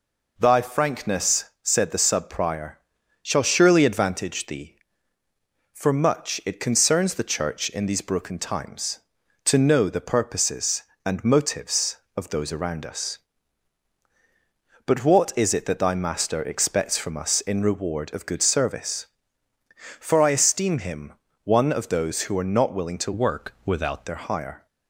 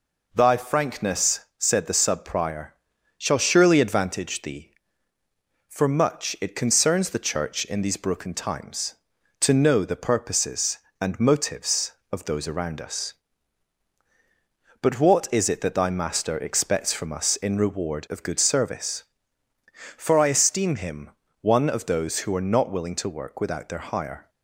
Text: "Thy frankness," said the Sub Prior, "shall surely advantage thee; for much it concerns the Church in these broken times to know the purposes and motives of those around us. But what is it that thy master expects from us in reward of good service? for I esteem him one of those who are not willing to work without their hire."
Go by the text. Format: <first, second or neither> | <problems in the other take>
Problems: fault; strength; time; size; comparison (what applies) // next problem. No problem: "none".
second | pauses between "him" and "one"; slight; at 21.1 s; 0.30 s long; slight in the second // changes voice from "work" to "without"; from 23.1 to 24.0 s; 0.9 s long